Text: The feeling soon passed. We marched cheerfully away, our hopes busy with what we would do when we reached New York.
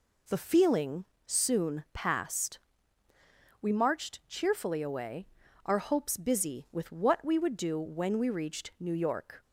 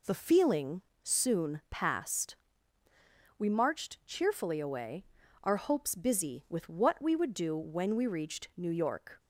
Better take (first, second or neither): neither